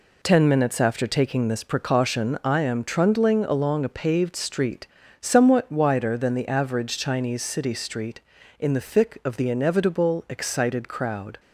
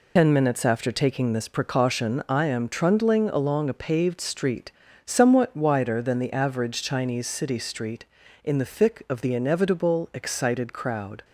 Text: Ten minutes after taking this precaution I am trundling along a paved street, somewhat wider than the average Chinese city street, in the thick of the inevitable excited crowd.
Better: first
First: none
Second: loses the start of "Ten"; at 0.1 s; 75 ms

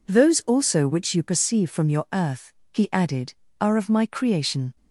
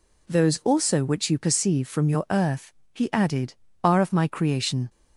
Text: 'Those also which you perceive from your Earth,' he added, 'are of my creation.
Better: neither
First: none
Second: none

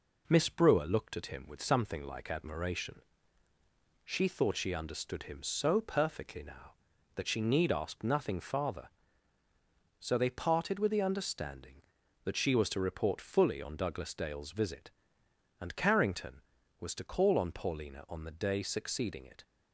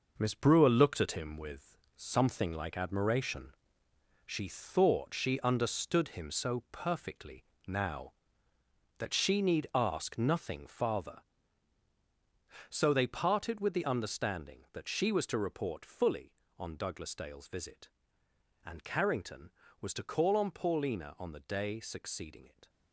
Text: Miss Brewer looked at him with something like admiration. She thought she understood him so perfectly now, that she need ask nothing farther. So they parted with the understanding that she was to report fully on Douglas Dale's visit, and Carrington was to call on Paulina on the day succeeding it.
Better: first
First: none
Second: gets quieter; strong; throughout; 7.5 dB // pauses between "with" and "something"; slight; at 1.7 s; 0.18 s long // pauses between "perfectly" and "now"; slight; at 7.4 s; 0.24 s long

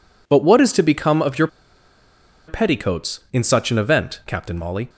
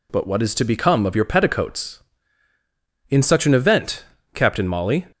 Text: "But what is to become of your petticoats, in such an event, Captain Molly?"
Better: second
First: pauses between "your" and "petticoats"; at 1.4 s; 1.0 s long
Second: none

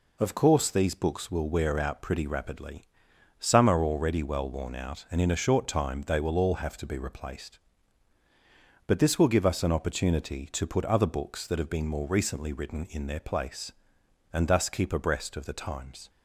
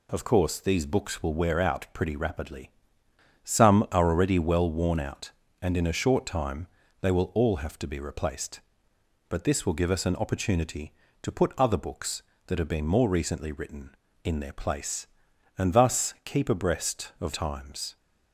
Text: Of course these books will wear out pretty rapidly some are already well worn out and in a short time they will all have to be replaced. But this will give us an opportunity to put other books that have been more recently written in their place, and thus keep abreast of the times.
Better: first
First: pauses between "rapidly" and "some"; noticeable; at 2.8 s; 0.56 s long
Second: pauses between "rapidly" and "some"; noticeable; at 2.7 s; 0.74 s long // pauses between "time" and "they"; slight; at 6.6 s; 0.34 s long // skips "the"; at 17.3 s

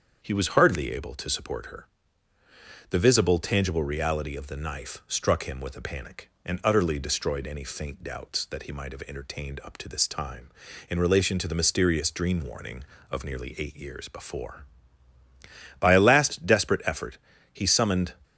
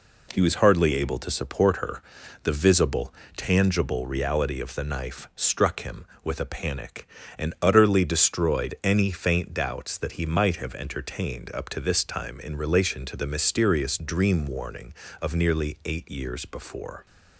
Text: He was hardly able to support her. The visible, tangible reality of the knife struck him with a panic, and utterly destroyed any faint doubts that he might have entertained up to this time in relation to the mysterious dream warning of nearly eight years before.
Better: second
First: starts louder than the rest; strong; until 1.2 s; 7 dB // goes on to say "By a last desperate effort he summoned"; strong; from 15.7 s on; 2.3 s long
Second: none

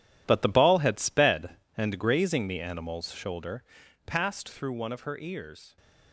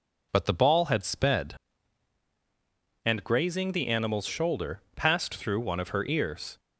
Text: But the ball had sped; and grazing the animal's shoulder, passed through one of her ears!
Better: second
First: gets quieter; strong; throughout; 12.5 dB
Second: none

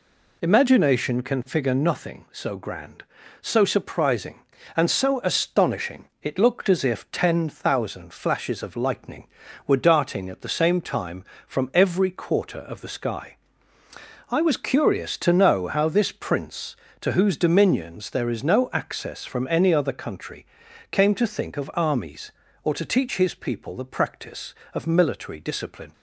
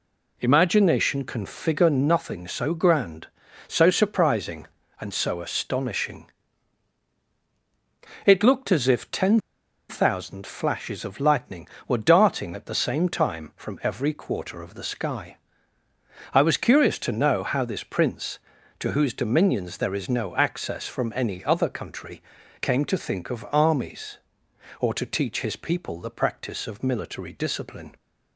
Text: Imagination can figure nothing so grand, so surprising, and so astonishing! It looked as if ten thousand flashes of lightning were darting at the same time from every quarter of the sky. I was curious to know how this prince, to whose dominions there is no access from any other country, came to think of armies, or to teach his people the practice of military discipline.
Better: first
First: none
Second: pauses between "ten" and "thousand"; noticeable; at 9.3 s; 0.49 s long

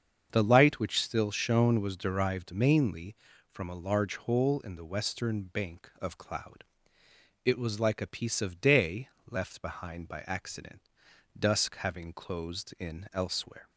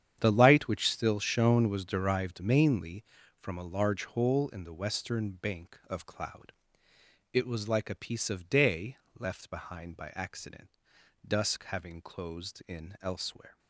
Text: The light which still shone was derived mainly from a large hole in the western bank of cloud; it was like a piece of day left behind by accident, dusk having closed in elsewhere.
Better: first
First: starts louder than the rest; until 1.3 s; 7 dB // pauses between "day" and "left"; slight; at 9.0 s; 0.22 s long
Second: gets quieter; strong; throughout; 13.5 dB // starts louder than the rest; strong; until 1.2 s; 9 dB // pauses between "day" and "left"; slight; at 8.9 s; 0.22 s long

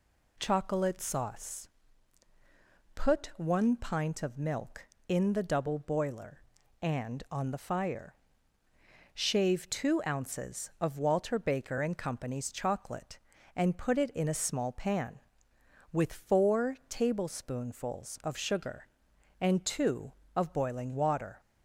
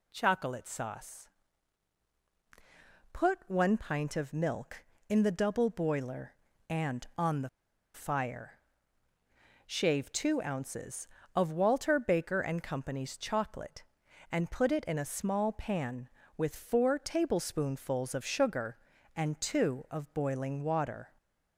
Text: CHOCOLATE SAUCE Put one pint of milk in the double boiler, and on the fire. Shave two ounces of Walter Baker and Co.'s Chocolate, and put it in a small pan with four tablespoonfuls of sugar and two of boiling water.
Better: first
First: pauses between "SAUCE" and "Put"; strong; at 1.6 s; 1.2 s long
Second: pauses between "SAUCE" and "Put"; strong; at 1.2 s; 1.8 s long // pauses between "the" and "fire"; at 7.4 s; 0.45 s long

